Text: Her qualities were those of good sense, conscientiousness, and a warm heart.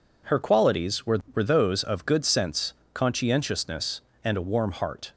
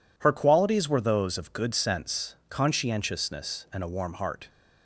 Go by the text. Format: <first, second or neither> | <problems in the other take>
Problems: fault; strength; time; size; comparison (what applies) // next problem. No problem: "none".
second | says "were" twice; at 1.3 s